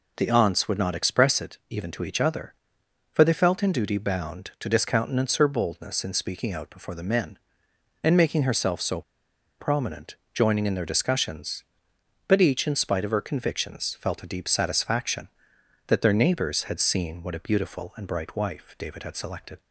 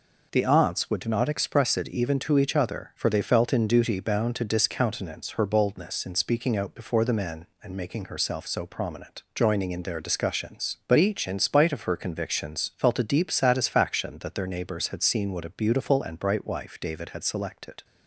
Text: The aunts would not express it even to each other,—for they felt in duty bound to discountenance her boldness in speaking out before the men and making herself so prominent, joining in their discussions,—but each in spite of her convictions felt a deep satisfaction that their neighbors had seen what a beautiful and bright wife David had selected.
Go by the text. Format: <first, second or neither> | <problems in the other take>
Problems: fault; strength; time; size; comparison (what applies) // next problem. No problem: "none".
second | pauses between "so" and "prominent"; noticeable; at 9.0 s; 0.57 s long